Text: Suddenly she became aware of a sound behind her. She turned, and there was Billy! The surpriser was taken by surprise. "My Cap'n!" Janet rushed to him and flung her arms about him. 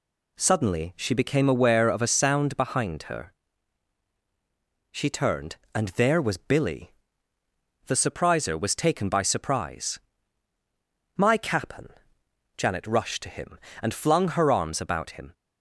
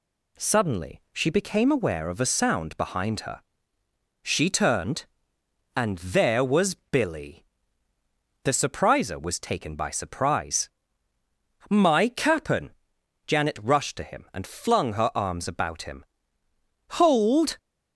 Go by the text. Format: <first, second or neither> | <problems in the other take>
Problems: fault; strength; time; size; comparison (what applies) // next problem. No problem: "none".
first | goes on to say "Hold"; from 16.9 s on; 0.60 s long